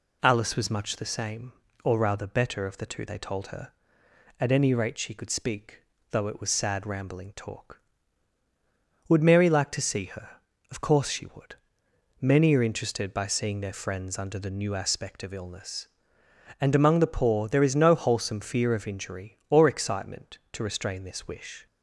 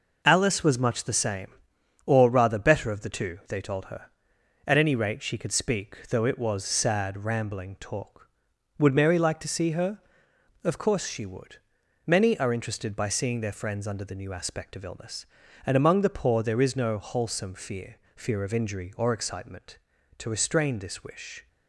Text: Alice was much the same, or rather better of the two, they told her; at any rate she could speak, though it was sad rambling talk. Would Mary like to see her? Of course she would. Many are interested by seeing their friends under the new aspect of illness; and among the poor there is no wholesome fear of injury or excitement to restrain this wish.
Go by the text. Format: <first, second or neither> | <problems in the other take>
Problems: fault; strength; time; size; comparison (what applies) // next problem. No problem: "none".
first | says "fear" twice; at 18.1 s